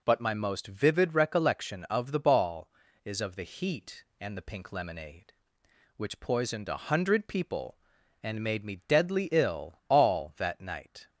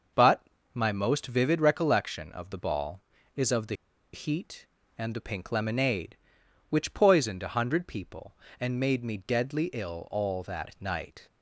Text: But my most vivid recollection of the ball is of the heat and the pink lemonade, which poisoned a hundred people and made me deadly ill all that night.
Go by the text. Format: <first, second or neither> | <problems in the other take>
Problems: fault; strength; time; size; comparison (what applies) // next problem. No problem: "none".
first | starts louder than the rest; noticeable; until 1.4 s; 6 dB // pauses between "But" and "my"; slight; at 0.4 s; 0.30 s long // pauses between "the" and "heat"; at 3.7 s; 0.40 s long